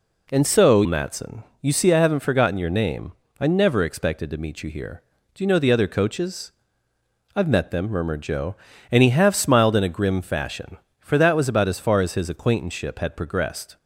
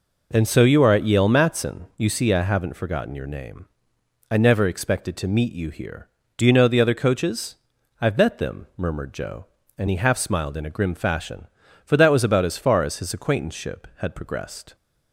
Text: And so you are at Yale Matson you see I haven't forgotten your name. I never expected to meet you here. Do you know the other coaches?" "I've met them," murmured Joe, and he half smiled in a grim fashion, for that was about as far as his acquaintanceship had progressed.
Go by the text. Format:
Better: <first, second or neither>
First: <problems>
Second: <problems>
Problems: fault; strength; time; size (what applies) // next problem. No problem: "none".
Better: second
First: skips "you are at Yale"; at 0.8 s // pauses between "Matson" and "you"; slight; at 1.4 s; 0.18 s long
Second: none